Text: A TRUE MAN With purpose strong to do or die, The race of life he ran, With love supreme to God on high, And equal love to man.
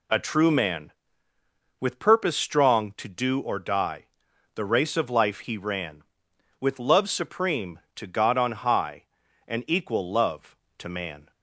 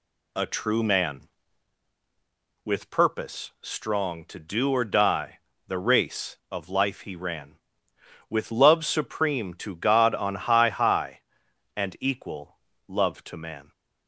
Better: first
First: none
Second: says "high" twice; at 10.6 s // pauses between "equal" and "love"; slight; at 12.5 s; 0.28 s long

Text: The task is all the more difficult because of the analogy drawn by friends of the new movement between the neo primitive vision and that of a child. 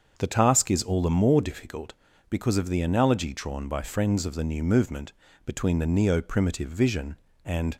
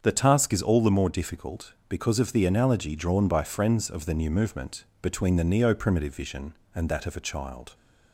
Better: second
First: starts louder than the rest; until 1.1 s; 7 dB // pauses between "movement" and "between"; slight; at 5.1 s; 0.32 s long // stops before "that of a child"; at 7.7 s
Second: starts louder than the rest; strong; until 1.0 s; 7.5 dB // pauses between "movement" and "between"; slight; at 4.8 s; 0.18 s long

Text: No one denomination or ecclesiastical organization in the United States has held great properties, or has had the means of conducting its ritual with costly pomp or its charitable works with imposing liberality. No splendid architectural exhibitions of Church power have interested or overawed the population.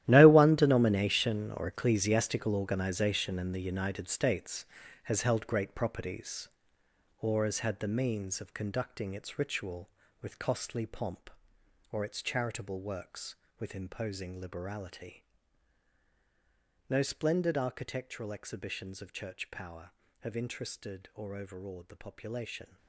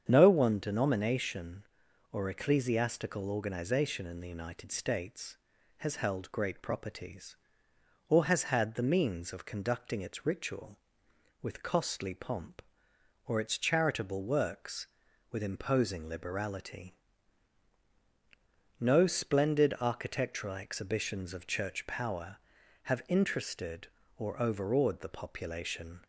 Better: second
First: gets quieter; strong; throughout; 14 dB // starts louder than the rest; strong; until 1.0 s; 13 dB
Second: starts louder than the rest; strong; until 1.0 s; 8 dB

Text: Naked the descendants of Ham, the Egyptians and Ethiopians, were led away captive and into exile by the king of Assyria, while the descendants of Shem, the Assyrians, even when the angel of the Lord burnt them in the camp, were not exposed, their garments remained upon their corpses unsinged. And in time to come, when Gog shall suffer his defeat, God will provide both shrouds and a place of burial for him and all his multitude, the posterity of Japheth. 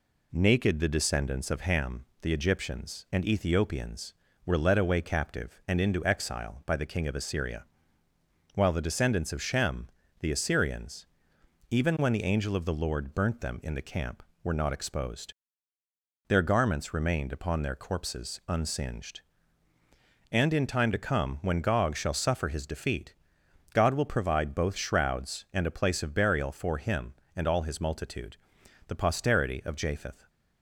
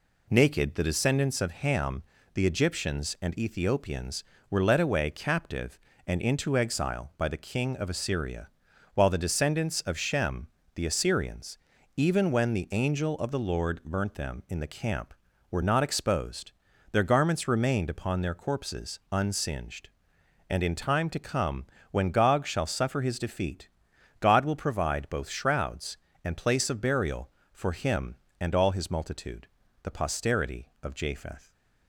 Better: first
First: none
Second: skips "a"; at 26.3 s

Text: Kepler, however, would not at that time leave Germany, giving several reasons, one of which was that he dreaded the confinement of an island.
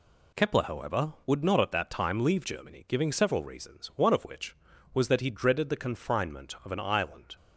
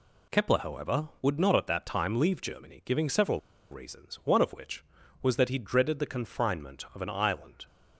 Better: first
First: none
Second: pauses between "several" and "reasons"; slight; at 3.3 s; 0.31 s long

